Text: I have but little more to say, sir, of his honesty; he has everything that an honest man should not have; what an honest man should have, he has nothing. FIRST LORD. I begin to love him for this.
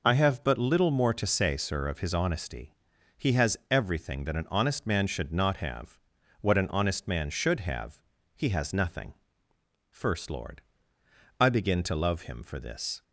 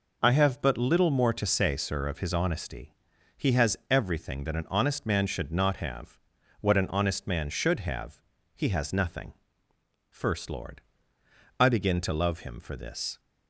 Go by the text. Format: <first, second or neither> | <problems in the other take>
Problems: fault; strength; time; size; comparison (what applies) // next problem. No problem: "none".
neither | none